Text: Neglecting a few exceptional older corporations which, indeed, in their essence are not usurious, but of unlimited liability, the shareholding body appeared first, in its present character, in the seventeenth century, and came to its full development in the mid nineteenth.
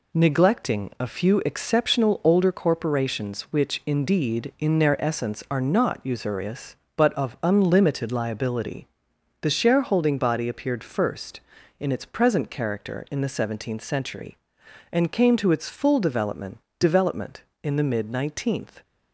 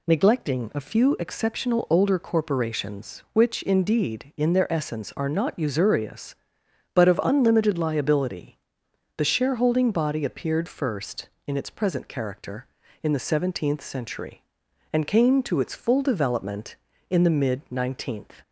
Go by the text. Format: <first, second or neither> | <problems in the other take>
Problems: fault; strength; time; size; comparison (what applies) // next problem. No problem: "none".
second | says "development" twice; at 16.7 s